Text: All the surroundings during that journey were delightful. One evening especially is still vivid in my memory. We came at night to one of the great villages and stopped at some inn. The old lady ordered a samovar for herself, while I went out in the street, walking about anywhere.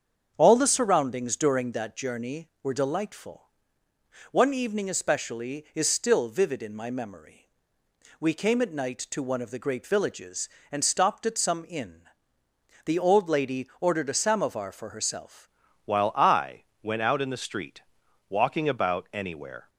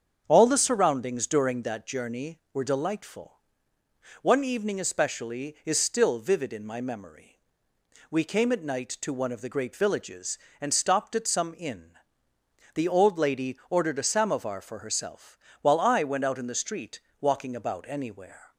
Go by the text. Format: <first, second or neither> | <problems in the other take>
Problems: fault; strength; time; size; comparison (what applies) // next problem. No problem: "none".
second | starts louder than the rest; strong; until 1.3 s; 7.5 dB; strong in the second // changes voice at "while"; from 15.8 s on; 3.8 s long // pauses between "I" and "went"; slight; at 16.6 s; 0.20 s long